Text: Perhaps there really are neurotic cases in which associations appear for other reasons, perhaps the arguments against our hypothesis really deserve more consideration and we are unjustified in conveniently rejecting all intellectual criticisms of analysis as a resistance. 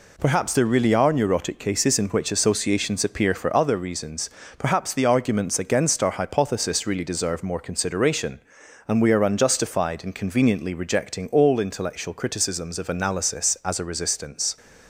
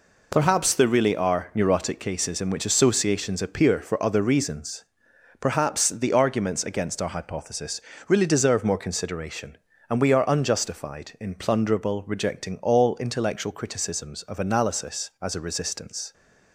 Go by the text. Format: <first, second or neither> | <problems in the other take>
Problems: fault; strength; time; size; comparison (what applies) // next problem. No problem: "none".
first | pauses between "hypothesis" and "really"; slight; at 7.8 s; 0.28 s long // says "plunderable" for "conveniently"; at 11.3 s